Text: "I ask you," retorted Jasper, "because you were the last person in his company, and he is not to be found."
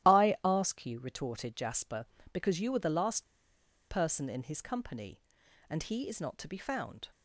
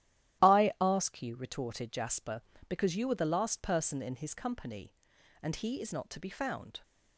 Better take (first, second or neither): second